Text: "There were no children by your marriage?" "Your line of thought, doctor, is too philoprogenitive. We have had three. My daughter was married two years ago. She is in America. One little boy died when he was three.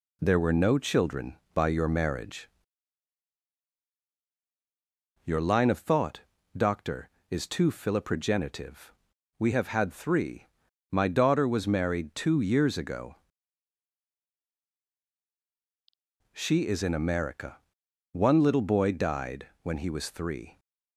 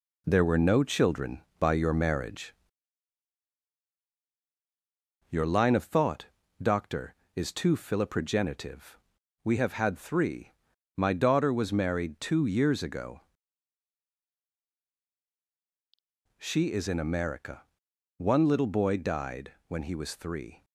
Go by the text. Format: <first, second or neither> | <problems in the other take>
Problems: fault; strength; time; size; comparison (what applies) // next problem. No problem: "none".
first | gets quieter; noticeable; throughout; 4.5 dB // pauses between "died" and "when"; slight; at 19.5 s; 0.16 s long; slight in the first